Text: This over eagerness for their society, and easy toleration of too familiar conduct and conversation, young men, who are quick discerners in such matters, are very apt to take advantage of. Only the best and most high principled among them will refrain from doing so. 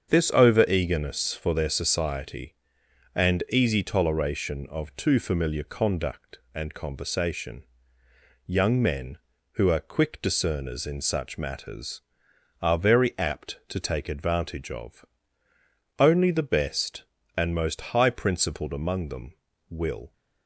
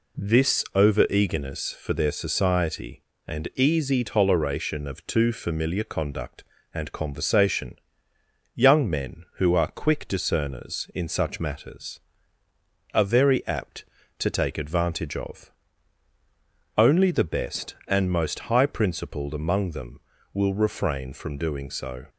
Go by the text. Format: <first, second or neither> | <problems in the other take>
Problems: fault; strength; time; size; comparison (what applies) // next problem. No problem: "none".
second | starts louder than the rest; strong; until 1.1 s; 7.5 dB // stops before "refrain from doing so"; at 20.1 s